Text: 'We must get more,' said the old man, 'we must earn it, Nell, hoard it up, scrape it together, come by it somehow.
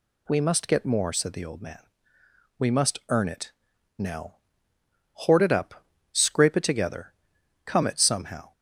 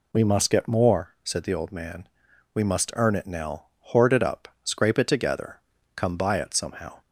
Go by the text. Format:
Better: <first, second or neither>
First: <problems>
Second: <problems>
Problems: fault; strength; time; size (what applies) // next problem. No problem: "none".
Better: second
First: skips "by"; at 7.8 s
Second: none